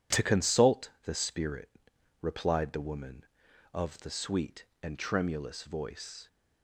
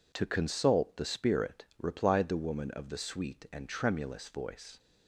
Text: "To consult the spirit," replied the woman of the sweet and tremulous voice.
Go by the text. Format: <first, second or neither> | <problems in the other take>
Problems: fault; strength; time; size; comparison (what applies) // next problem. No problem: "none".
neither | none